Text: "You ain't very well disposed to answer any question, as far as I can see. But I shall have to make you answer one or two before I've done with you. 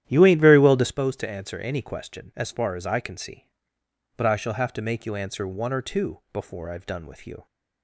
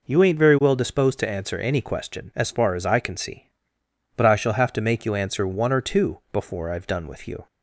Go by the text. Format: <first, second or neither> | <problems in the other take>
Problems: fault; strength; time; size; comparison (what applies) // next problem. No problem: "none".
second | starts louder than the rest; strong; until 0.9 s; 11 dB